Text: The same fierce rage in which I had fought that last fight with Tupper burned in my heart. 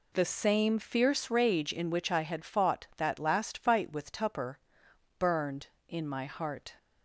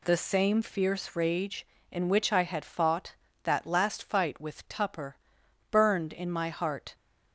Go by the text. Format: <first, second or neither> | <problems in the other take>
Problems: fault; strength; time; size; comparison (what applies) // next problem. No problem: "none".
neither | pauses between "Tupper" and "burned"; noticeable; the same in both